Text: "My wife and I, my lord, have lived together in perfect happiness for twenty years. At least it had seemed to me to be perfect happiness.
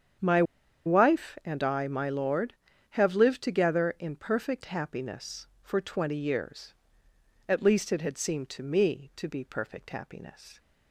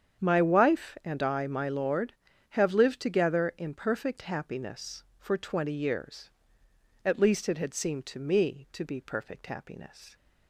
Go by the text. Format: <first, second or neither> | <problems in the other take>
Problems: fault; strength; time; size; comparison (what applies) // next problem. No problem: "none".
second | starts louder than the rest; strong; until 1.7 s; 8 dB; strong in the second // pauses between "My" and "wife"; at 0.4 s; 0.43 s long